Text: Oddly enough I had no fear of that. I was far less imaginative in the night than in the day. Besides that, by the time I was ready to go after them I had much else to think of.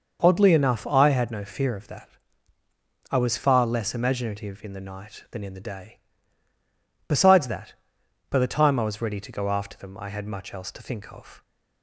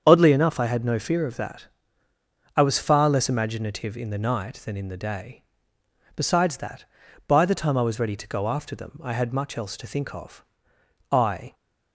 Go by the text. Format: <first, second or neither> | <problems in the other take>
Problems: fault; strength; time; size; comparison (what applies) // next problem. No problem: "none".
first | starts louder than the rest; strong; until 1.0 s; 7.5 dB; noticeable in the first // goes on to say "I"; slight; from 11.0 s on; 0.44 s long